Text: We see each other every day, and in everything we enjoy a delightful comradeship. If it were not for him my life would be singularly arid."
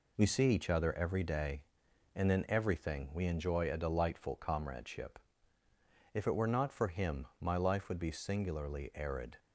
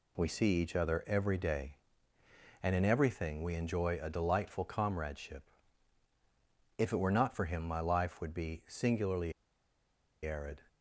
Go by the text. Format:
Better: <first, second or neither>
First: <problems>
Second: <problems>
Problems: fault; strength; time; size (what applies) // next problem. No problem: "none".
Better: first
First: none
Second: pauses between "singularly" and "arid"; noticeable; at 9.3 s; 0.92 s long